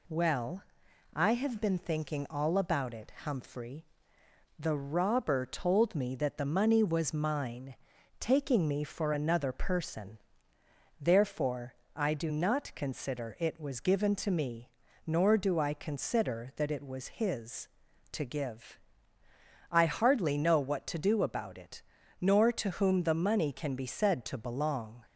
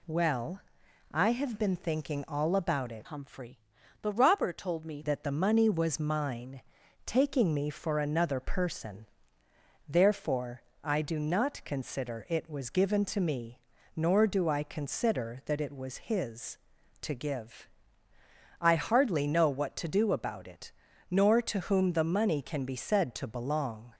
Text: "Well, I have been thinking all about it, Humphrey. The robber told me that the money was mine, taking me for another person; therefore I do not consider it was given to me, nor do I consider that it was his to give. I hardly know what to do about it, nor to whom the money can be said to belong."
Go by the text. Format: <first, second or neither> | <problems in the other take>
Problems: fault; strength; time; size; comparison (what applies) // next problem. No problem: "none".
first | changes voice from "Humphrey" to "me"; from 3.0 to 5.0 s; 2.0 s long // pauses between "therefore" and "I"; slight; at 10.6 s; 0.24 s long; slight in the first